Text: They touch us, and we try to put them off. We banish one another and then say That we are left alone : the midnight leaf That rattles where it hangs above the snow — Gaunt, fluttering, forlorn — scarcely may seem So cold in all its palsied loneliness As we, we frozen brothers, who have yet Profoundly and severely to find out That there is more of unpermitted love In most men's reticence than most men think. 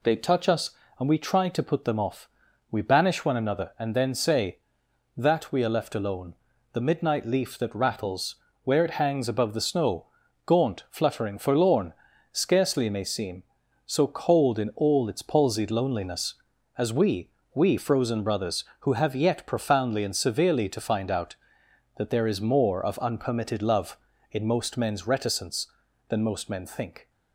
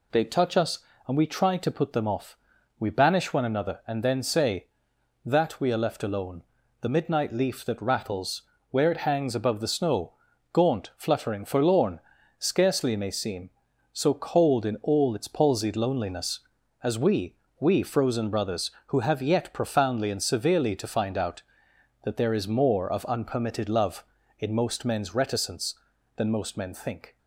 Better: neither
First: pauses between "rattles" and "where"; slight; at 8.3 s; 0.30 s long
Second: pauses between "rattles" and "where"; slight; at 8.4 s; 0.30 s long

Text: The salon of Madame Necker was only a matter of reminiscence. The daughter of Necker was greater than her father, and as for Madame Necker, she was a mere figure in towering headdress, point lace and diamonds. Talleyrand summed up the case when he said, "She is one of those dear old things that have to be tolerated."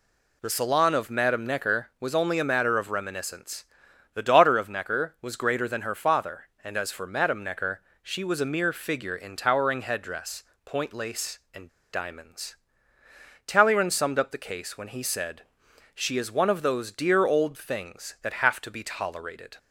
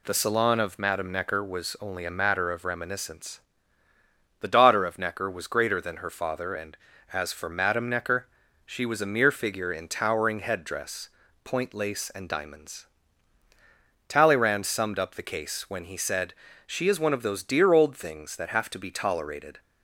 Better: second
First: pauses between "and" and "diamonds"; slight; at 11.6 s; 0.25 s long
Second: none

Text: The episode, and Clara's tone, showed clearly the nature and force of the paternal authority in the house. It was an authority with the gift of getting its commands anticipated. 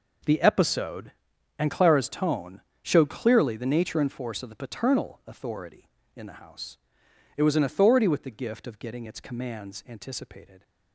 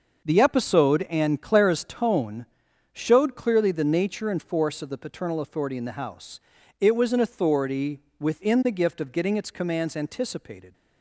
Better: first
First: none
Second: starts louder than the rest; noticeable; until 1.3 s; 6 dB // says "within" for "with"; at 8.2 s

